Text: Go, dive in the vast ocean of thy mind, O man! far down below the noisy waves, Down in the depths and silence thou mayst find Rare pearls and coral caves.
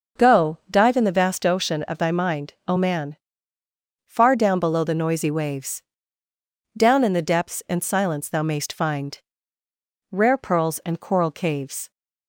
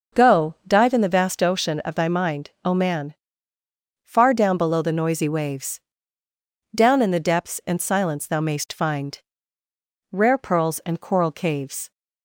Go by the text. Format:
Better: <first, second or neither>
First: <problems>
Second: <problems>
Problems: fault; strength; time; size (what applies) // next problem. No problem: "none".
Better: neither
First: pauses between "find" and "Rare"; noticeable; at 9.1 s; 0.94 s long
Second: pauses between "find" and "Rare"; noticeable; at 9.1 s; 0.94 s long